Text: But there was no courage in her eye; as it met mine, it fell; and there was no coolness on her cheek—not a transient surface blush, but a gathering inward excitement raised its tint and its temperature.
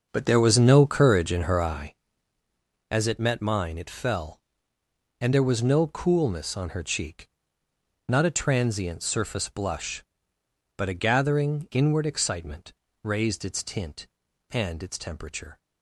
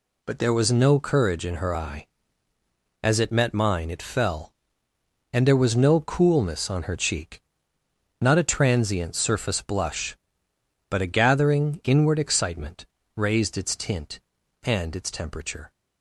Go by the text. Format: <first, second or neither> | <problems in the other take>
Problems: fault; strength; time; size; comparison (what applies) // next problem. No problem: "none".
second | starts louder than the rest; until 2.0 s; 6.5 dB // pauses between "excitement" and "raised"; slight; at 12.7 s; 0.32 s long; slight in the second